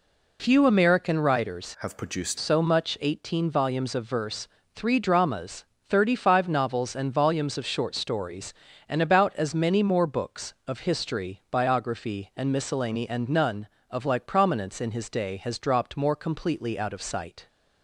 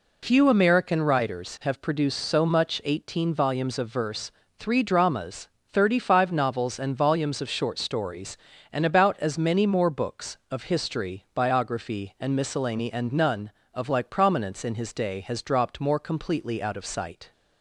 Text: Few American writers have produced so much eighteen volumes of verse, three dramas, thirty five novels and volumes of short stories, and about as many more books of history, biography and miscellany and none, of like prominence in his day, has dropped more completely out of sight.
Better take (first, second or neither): second